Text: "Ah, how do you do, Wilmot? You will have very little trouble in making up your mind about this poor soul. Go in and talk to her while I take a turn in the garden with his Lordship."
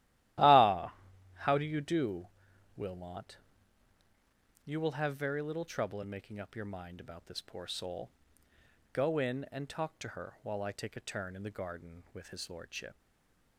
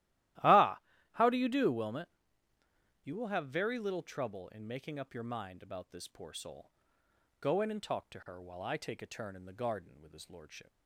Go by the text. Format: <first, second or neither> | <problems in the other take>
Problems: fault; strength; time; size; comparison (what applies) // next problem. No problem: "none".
second | starts louder than the rest; strong; until 1.8 s; 15 dB; strong in the second // stays silent after the last word; slight; from 12.9 s on; 0.6 s long